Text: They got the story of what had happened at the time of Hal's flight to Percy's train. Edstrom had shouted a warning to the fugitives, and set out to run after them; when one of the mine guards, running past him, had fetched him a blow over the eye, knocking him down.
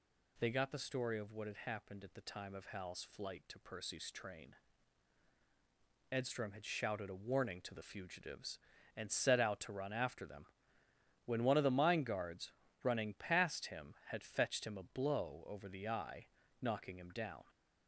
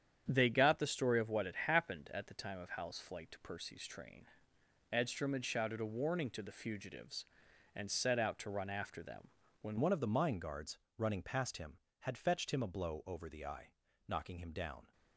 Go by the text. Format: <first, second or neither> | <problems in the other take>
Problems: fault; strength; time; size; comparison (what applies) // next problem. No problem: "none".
first | starts louder than the rest; strong; until 1.2 s; 8.5 dB // changes voice at "one"; from 9.7 s on; 5.2 s long